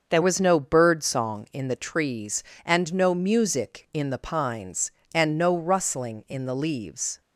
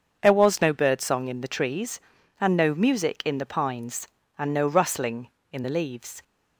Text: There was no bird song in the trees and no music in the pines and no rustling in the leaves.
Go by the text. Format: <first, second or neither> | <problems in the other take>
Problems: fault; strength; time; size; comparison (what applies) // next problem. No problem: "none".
second | starts louder than the rest; until 1.1 s; 6.5 dB; also in the second // changes voice at "was"; from 0.2 s on; 7.0 s long